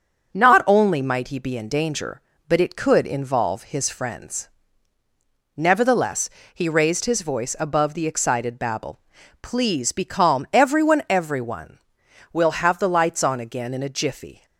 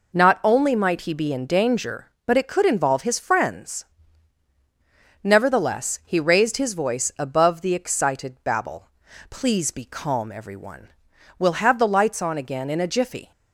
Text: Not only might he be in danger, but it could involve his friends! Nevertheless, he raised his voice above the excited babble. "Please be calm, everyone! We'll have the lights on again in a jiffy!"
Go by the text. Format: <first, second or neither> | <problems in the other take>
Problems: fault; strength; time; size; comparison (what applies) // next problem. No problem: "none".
second | starts louder than the rest; until 1.3 s; 6.5 dB // says "everyone" twice; at 11.0 s